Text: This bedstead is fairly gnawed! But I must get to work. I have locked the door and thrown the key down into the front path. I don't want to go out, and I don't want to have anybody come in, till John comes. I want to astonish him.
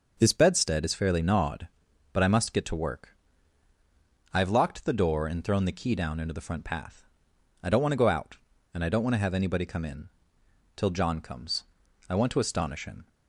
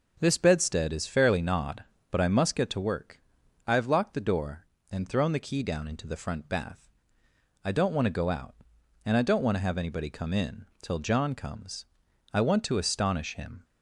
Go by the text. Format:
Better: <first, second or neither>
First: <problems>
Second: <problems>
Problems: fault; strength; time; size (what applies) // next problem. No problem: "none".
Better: first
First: none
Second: starts louder than the rest; noticeable; until 1.2 s; 6 dB // says "bath" for "path"; at 6.4 s